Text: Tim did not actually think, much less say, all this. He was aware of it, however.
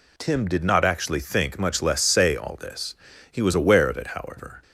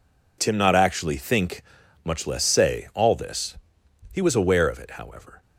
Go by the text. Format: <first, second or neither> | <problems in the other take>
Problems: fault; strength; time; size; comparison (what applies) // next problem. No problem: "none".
first | skips "did"; at 0.5 s